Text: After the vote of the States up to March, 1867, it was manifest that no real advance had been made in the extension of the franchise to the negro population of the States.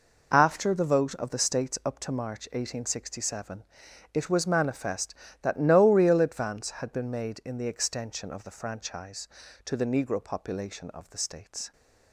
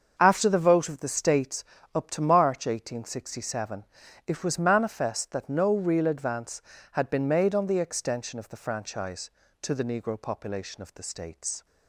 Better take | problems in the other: first | starts louder than the rest; until 1.2 s; 6.5 dB // pauses between "States" and "up"; slight; at 1.6 s; 0.28 s long // says "on" for "in"; at 7.5 s

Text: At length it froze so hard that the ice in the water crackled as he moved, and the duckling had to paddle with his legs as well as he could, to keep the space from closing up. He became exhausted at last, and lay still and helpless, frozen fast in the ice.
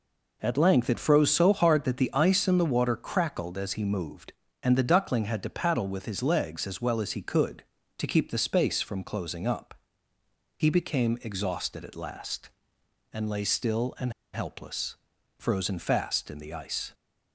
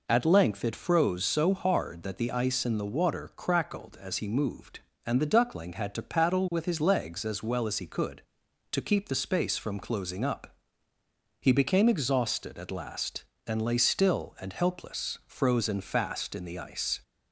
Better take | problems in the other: second | pauses between "and" and "helpless"; slight; at 14.1 s; 0.20 s long

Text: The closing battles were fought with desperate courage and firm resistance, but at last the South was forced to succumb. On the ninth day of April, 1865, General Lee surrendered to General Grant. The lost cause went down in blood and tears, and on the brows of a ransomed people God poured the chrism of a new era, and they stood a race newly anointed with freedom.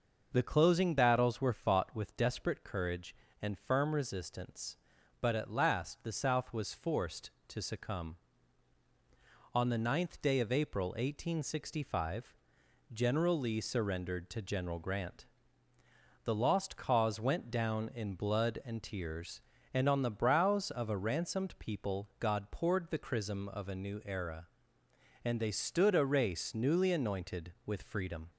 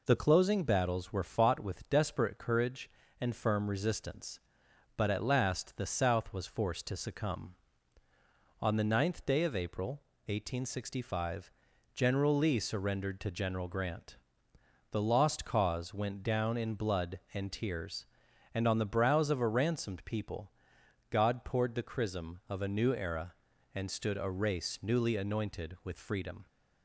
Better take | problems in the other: first | pauses between "people" and "God"; noticeable; at 20.4 s; 0.62 s long // skips "they"; at 23.8 s

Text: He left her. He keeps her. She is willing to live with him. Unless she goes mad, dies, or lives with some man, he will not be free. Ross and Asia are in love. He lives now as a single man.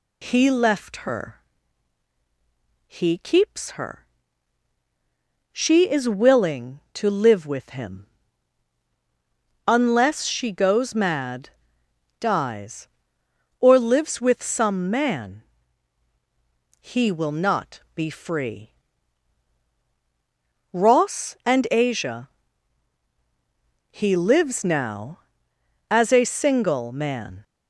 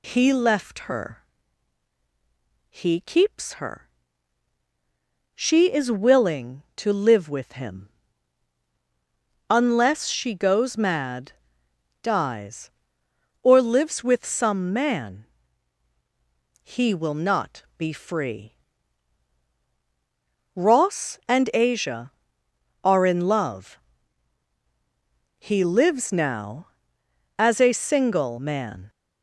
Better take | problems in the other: second | pauses between "not" and "be"; slight; at 17.8 s; 0.16 s long; slight in the second // skips "are in love"; at 23.0 s

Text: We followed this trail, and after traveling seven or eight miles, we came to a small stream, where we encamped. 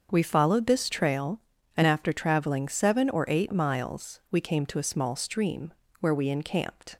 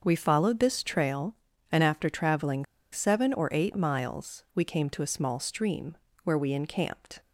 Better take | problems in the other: first | starts louder than the rest; until 1.0 s; 6.5 dB; also in the first // pauses between "traveling" and "seven"; slight; at 2.6 s; 0.26 s long

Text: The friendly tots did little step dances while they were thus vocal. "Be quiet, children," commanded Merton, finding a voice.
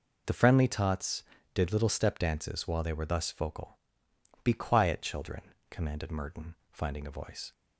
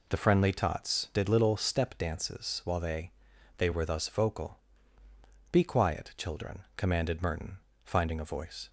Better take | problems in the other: first | says "they" twice; at 3.5 s

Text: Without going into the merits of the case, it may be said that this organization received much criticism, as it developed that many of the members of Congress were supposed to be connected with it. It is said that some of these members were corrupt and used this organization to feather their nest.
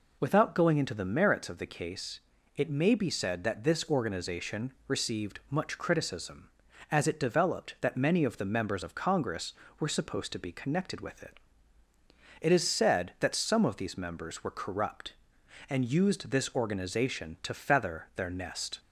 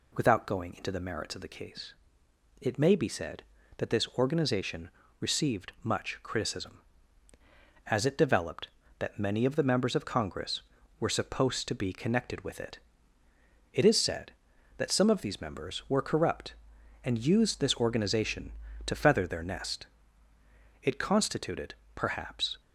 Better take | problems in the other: first | pauses between "organization" and "received"; slight; at 4.8 s; 0.30 s long // goes on to say "It constituted perhaps"; strong; from 20.8 s on; 1.7 s long

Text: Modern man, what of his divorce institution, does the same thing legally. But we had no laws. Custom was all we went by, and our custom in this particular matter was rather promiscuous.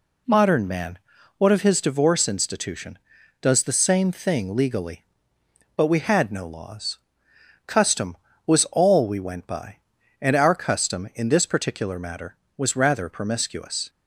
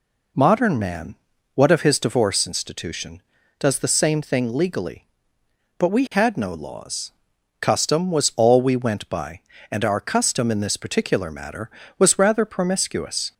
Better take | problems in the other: neither | none

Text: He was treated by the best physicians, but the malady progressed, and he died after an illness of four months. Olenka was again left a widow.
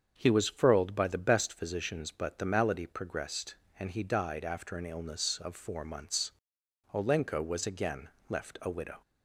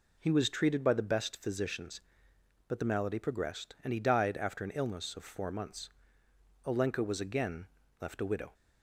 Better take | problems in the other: second | starts louder than the rest; strong; until 1.1 s; 7 dB // says "furled" for "treated"; at 0.4 s // pauses between "again" and "left"; slight; at 8.0 s; 0.22 s long; slight in the second

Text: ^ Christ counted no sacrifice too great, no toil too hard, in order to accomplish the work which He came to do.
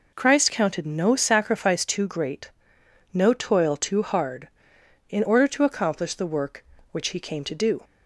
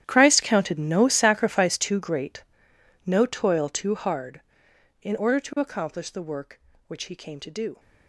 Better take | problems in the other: first | gets quieter; strong; throughout; 18 dB

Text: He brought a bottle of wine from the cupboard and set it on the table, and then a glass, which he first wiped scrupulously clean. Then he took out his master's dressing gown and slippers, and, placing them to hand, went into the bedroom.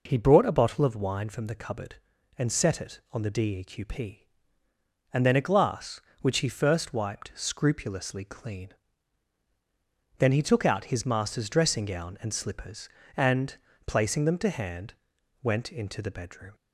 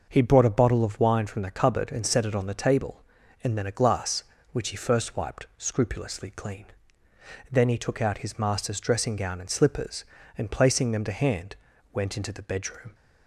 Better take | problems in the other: second | says "deqp" for "table"; at 3.3 s

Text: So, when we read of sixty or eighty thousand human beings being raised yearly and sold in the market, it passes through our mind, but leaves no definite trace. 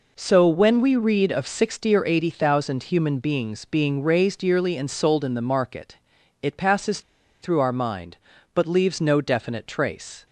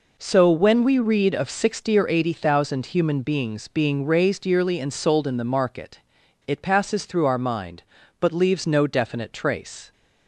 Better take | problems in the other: second | pauses between "passes" and "through"; at 7.0 s; 0.41 s long

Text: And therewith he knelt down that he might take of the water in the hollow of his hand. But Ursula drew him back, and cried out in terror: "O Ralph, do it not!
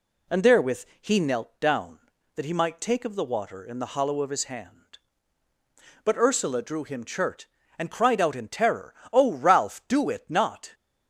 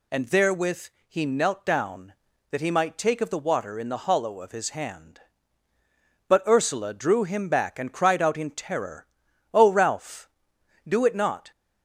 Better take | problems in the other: second | pauses between "therewith" and "he"; slight; at 0.8 s; 0.16 s long; slight in the second // says "chert" for "back"; at 7.0 s

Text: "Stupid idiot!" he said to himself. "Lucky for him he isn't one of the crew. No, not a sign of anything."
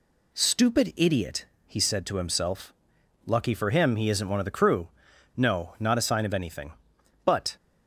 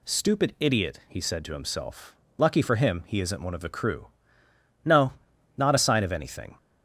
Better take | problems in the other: second | goes on to say "But"; slight; from 7.2 s on; 0.32 s long

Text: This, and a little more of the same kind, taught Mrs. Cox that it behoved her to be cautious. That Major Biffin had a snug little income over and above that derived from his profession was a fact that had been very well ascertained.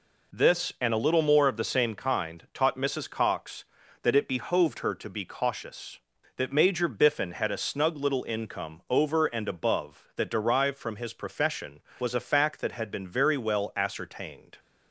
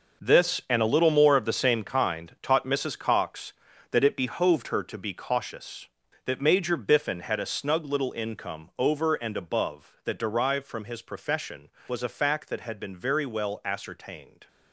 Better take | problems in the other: first | gets quieter; strong; throughout; 12 dB

